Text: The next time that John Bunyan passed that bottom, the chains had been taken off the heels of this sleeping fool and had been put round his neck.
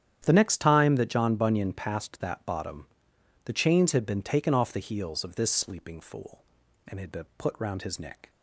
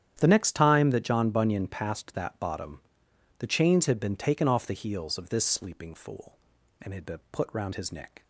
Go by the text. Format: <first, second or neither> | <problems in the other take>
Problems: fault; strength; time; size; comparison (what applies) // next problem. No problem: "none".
neither | starts louder than the rest; strong; the same in both